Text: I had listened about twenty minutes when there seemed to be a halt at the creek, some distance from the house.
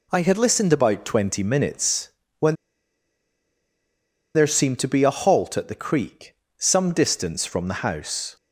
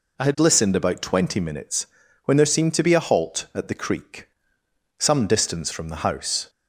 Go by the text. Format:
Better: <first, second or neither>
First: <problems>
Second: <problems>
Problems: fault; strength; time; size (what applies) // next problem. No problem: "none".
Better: second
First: pauses between "minutes" and "when"; slight; at 2.0 s; 0.30 s long // pauses between "when" and "there"; strong; at 2.5 s; 1.8 s long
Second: pauses between "minutes" and "when"; at 1.8 s; 0.38 s long